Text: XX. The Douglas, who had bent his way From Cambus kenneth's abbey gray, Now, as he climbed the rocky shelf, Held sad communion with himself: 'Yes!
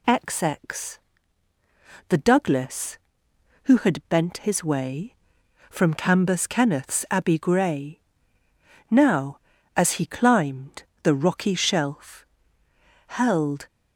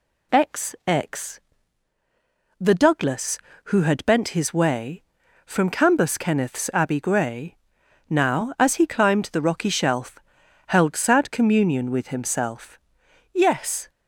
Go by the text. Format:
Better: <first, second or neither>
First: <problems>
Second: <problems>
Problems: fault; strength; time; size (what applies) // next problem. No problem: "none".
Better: second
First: pauses between "climbed" and "the"; slight; at 10.8 s; 0.20 s long // stops before "sad communion with himself Yes"; at 13.6 s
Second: none